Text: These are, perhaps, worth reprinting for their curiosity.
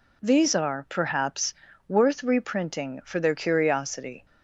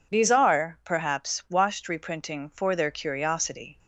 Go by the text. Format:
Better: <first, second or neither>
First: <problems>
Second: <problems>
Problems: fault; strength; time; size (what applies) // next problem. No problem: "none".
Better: first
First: none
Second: says "washed" for "worth"; at 1.5 s